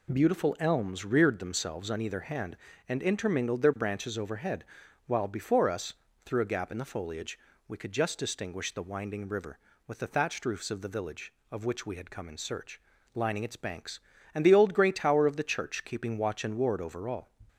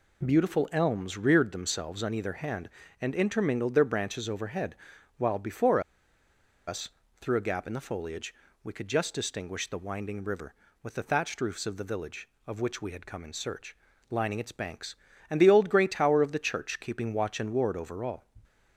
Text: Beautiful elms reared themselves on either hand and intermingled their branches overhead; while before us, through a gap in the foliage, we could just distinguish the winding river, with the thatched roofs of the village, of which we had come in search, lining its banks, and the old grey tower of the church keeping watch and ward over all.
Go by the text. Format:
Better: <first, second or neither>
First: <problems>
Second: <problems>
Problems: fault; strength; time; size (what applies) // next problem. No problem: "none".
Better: first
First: none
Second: pauses between "before" and "us"; noticeable; at 5.7 s; 0.87 s long